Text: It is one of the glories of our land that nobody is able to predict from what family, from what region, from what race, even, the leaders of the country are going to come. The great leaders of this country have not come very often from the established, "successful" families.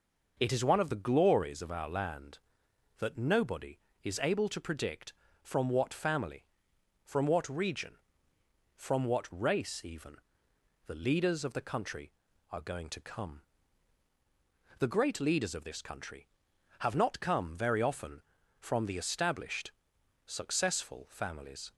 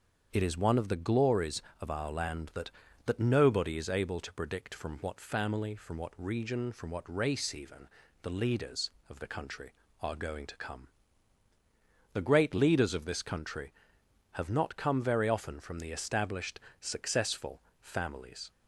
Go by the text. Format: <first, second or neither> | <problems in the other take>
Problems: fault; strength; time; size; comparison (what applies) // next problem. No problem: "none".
first | starts louder than the rest; until 1.3 s; 7 dB // says "that" twice; at 3.0 s // pauses between "successful" and "families"; slight; at 17.6 s; 0.18 s long